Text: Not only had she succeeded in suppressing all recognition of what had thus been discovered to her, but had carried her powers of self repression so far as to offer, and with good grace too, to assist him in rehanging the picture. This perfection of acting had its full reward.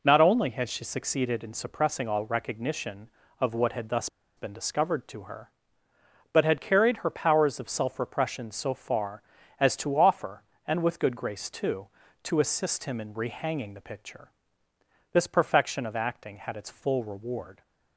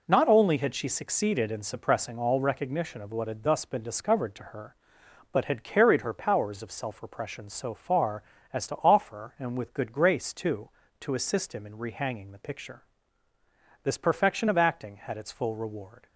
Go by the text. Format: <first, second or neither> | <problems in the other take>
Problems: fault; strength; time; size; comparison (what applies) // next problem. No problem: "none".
second | pauses between "thus" and "been"; slight; at 4.0 s; 0.28 s long